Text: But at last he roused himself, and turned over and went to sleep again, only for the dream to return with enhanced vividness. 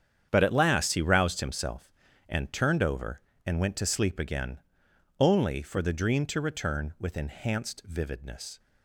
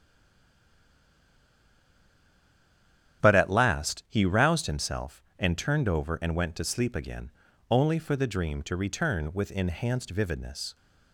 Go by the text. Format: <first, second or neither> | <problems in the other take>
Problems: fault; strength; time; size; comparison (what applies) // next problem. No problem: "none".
first | stays silent before the first word; strong; until 3.1 s; 3.1 s long // starts louder than the rest; strong; until 4.2 s; 9.5 dB; strong in the first